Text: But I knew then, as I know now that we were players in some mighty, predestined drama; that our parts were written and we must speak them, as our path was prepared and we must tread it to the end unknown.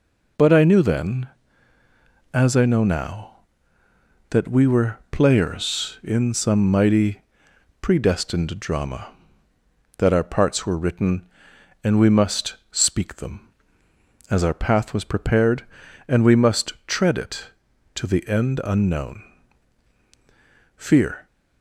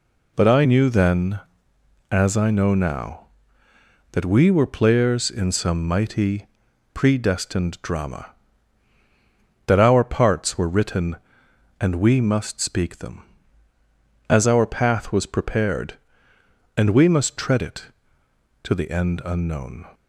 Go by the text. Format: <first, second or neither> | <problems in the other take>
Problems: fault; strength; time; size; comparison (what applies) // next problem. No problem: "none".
second | pauses between "must" and "speak"; slight; at 12.5 s; 0.16 s long // goes on to say "Fear"; from 20.7 s on; 0.50 s long